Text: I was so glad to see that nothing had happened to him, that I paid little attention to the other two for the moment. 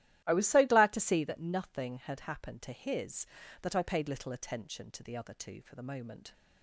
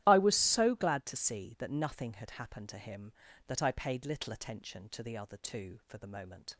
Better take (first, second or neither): second